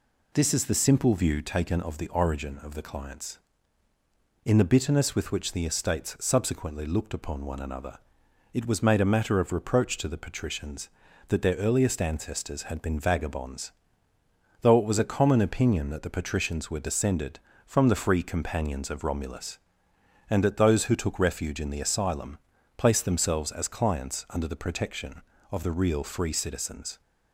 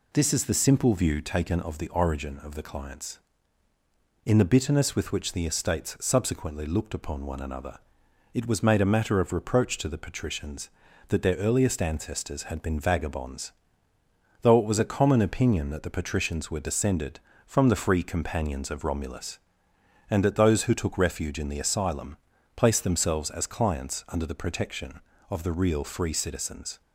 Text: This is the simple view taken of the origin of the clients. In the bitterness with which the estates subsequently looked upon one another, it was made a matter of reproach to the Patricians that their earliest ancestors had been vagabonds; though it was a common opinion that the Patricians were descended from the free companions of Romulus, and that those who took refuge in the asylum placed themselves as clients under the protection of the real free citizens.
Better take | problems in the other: neither | pauses between "asylum" and "placed"; the same in both

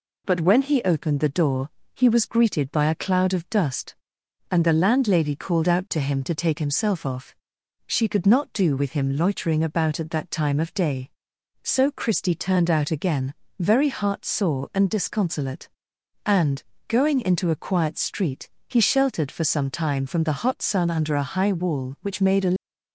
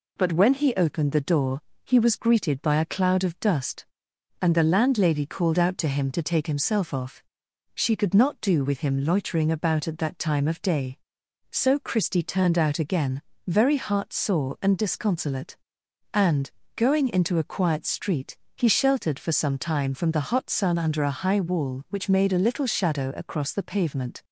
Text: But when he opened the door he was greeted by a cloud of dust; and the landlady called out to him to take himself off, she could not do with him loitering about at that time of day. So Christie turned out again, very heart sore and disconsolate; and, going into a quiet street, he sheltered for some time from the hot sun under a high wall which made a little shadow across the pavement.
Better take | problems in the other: second | pauses between "door" and "he"; slight; at 1.6 s; 0.28 s long; slight in the second // stops before "little shadow across the pavement"; at 22.5 s

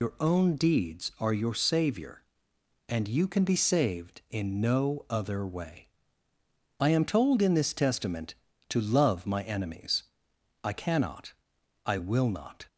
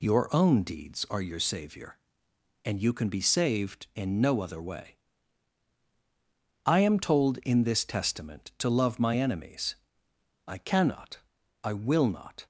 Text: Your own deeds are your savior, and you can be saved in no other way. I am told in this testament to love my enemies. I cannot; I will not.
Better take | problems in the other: second | loses the start of "Your"; at 0.0 s; 70 ms

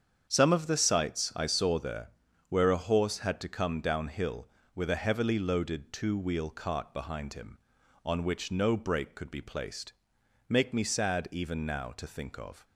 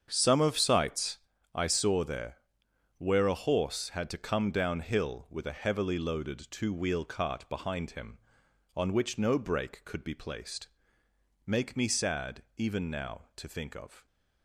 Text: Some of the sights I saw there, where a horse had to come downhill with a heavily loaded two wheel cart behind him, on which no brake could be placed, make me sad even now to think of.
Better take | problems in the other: first | starts louder than the rest; strong; until 1.1 s; 7.5 dB; strong in the first // skips "the"; at 0.5 s // pauses between "sights" and "I"; slight; at 1.1 s; 0.34 s long // pauses between "sad" and "even"; slight; at 12.4 s; 0.16 s long

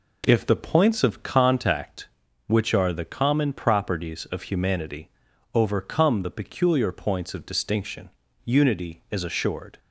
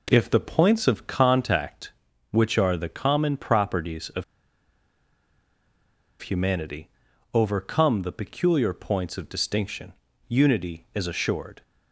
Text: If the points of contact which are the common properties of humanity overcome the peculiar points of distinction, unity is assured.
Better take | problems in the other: first | pauses between "of" and "humanity"; strong; at 4.2 s; 1.9 s long // pauses between "humanity" and "overcome"; at 6.9 s; 0.42 s long; also in the first

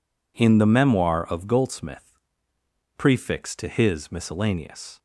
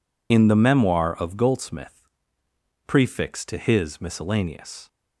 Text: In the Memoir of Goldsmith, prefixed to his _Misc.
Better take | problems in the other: first | loses the start of "In"; at 0.3 s; 45 ms

